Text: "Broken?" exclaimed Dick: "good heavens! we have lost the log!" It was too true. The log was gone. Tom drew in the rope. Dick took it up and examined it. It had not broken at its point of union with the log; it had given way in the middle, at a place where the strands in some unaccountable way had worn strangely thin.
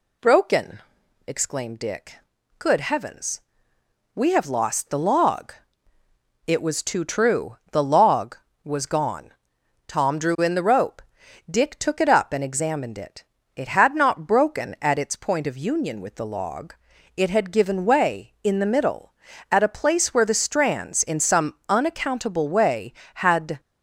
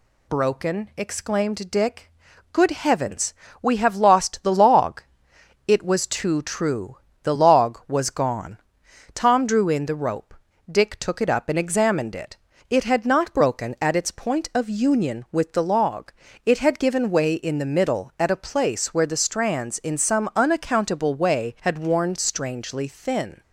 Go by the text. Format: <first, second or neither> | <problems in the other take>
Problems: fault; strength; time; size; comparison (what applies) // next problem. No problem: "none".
second | stops before "worn strangely thin"; at 23.5 s